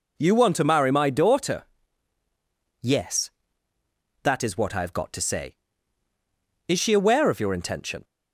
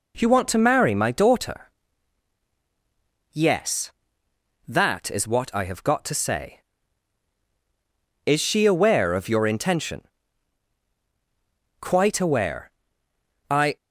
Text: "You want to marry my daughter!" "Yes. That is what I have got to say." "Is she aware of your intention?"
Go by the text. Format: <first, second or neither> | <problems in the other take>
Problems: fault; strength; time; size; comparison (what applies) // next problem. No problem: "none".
first | goes on to say "Quite aware I"; strong; from 11.7 s on; 1.9 s long